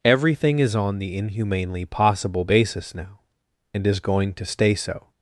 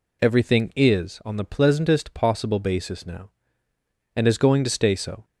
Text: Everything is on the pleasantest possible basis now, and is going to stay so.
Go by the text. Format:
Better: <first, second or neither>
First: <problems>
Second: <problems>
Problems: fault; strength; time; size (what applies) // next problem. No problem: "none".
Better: second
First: says "inhumanely" for "pleasantest"; at 1.1 s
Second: none